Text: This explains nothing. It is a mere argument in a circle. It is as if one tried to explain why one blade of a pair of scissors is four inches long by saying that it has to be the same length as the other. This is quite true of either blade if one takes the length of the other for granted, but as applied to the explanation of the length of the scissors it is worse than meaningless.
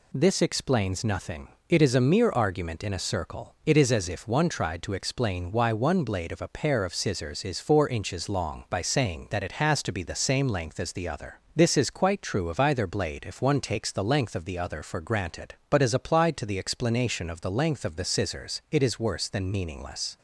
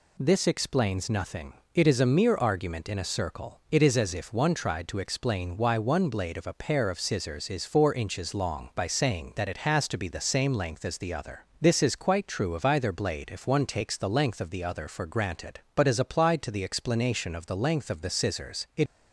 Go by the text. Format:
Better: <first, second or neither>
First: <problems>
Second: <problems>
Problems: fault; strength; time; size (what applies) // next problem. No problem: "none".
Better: first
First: none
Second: stops before "is worse than meaningless"; at 18.8 s